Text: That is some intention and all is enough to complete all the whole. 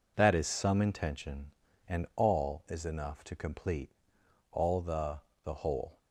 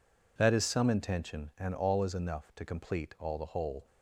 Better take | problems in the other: second | pauses between "complete" and "all"; noticeable; at 3.9 s; 0.62 s long // says "the" twice; at 5.4 s

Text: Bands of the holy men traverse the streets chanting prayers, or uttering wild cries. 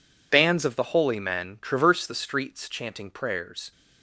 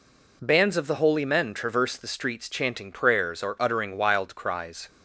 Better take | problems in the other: second | stops before "or uttering wild cries"; at 3.7 s

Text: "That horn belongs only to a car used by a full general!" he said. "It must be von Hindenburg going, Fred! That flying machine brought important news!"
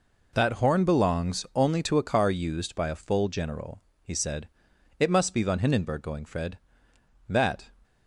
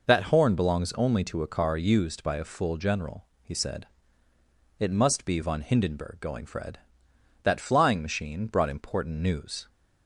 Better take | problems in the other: second | stops before "flying machine brought important news"; at 7.8 s

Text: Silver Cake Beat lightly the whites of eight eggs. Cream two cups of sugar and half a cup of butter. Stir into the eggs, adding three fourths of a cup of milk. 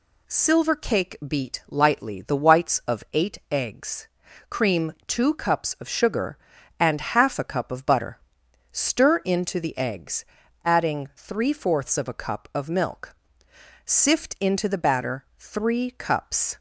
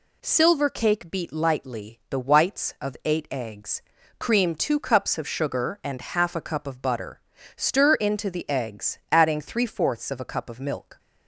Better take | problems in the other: second | goes on to say "Sift into the batter three cups"; strong; from 13.8 s on; 2.7 s long

